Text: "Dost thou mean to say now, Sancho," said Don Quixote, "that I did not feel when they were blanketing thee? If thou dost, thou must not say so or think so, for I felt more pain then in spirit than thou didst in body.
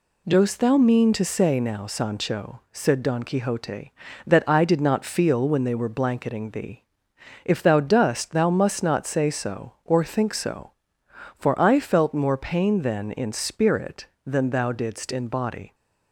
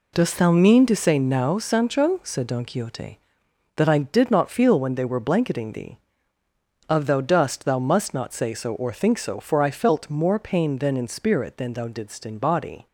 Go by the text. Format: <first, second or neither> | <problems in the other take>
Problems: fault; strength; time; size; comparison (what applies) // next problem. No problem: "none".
first | says "Of" for "If"; at 6.8 s